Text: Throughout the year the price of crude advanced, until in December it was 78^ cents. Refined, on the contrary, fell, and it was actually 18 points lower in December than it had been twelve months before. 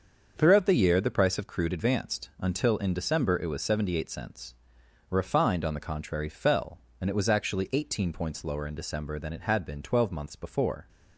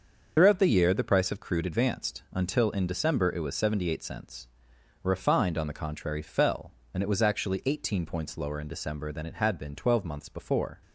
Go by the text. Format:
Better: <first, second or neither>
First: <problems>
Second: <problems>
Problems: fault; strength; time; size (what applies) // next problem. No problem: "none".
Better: first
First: starts louder than the rest; until 1.3 s; 6.5 dB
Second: loses the start of "Throughout"; at 0.3 s; 60 ms // starts louder than the rest; until 1.3 s; 6.5 dB